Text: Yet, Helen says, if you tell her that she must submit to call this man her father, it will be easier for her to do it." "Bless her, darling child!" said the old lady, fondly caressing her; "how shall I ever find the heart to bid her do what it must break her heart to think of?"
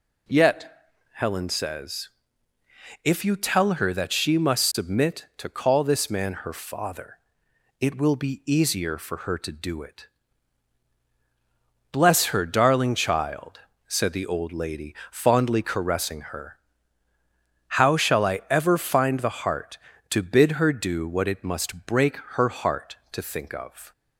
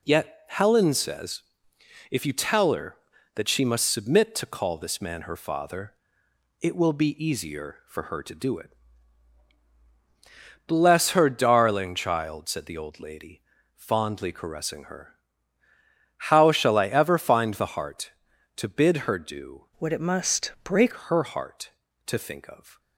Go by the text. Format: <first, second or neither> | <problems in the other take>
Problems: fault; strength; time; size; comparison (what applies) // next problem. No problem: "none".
first | changes voice from "what" to "break"; from 19.7 to 20.9 s; 1.2 s long